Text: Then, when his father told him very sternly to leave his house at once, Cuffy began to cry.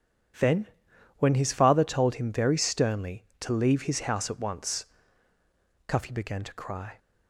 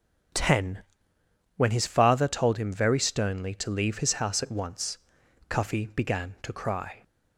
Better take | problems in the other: first | starts louder than the rest; strong; until 2.1 s; 8 dB // says "Ten" for "Then"; at 0.3 s

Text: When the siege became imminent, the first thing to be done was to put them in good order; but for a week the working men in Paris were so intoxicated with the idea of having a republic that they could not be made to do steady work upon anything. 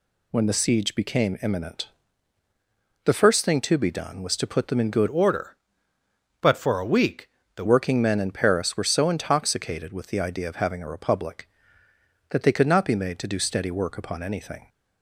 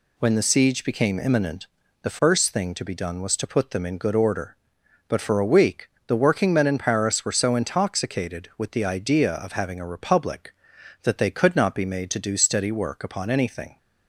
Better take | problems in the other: second | changes voice from "order" to "the"; from 5.0 to 7.6 s; 2.6 s long // pauses between "week" and "the"; slight; at 7.2 s; 0.28 s long; slight in the second

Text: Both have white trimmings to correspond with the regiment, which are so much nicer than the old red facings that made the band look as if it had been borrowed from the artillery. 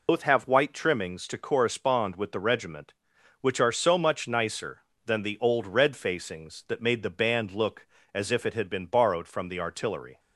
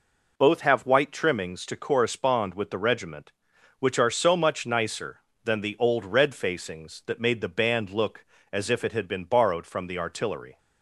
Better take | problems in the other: second | loses the start of "Both"; at 0.0 s; 100 ms

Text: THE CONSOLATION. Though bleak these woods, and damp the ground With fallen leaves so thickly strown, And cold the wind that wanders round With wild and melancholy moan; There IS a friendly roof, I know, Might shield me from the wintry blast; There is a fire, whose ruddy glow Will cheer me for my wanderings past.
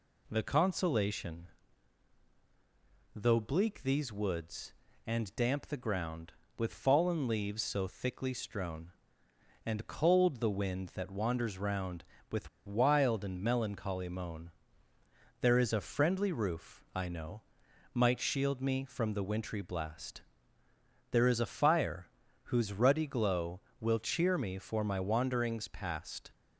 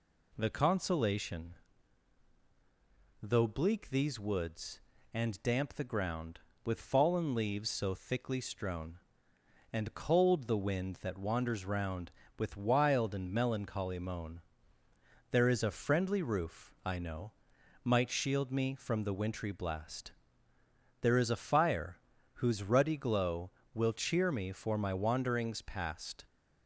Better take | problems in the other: second | pauses between "With" and "wild"; slight; at 12.4 s; 0.17 s long

